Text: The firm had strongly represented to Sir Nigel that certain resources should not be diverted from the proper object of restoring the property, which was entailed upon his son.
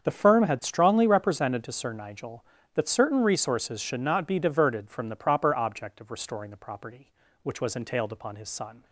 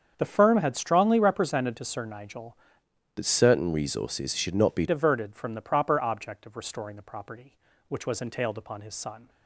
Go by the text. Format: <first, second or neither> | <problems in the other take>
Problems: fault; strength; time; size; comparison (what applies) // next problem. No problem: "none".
first | starts louder than the rest; strong; until 1.1 s; 7.5 dB; strong in the first // changes voice from "that" to "be"; from 3.1 to 4.8 s; 1.7 s long